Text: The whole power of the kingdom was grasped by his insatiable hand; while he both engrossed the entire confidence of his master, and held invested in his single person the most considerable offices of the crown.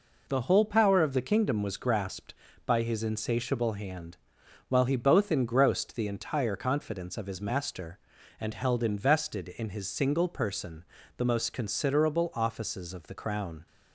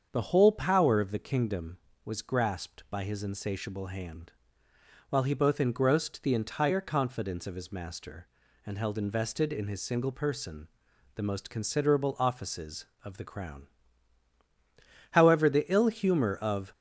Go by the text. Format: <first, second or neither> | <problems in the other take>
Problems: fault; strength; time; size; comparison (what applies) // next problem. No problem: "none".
first | starts louder than the rest; until 1.1 s; 7 dB // pauses between "person" and "the"; noticeable; at 10.6 s; 0.48 s long; slight in the first // goes on to say "However the ill humor of"; from 15.1 s on; 1.6 s long